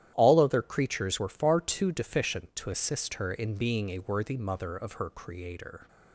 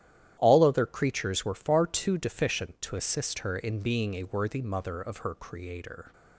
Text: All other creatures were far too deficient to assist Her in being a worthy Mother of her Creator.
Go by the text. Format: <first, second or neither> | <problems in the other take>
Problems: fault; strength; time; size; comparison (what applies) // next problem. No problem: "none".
neither | starts louder than the rest; strong; the same in both